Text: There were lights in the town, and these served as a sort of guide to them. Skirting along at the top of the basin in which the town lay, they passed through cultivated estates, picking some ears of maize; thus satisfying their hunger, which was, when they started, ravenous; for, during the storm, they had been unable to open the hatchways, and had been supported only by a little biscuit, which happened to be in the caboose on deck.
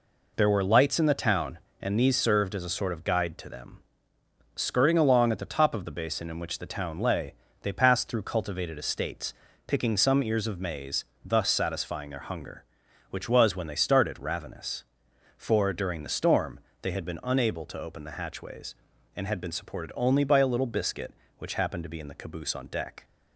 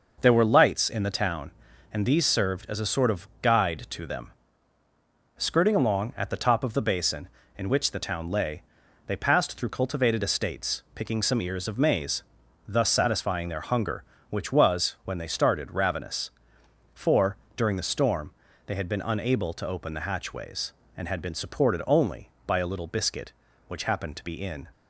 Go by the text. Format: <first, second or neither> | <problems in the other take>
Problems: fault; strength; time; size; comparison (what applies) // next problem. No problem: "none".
first | stops before "the caboose on deck"; at 24.7 s